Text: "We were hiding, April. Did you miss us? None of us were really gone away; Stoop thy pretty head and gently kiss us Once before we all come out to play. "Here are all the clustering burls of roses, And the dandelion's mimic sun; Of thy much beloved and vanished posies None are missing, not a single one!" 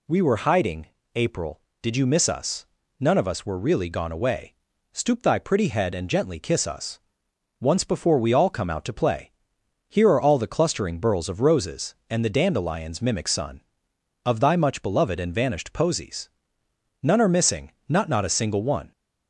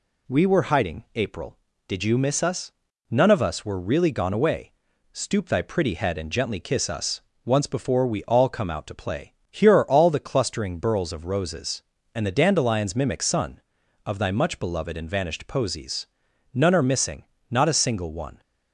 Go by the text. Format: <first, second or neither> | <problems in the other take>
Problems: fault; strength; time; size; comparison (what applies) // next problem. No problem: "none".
second | pauses between "us" and "Once"; noticeable; at 6.9 s; 0.60 s long; slight in the second // pauses between "posies" and "None"; noticeable; at 16.2 s; 0.72 s long; noticeable in the second // says "not" twice; at 18.0 s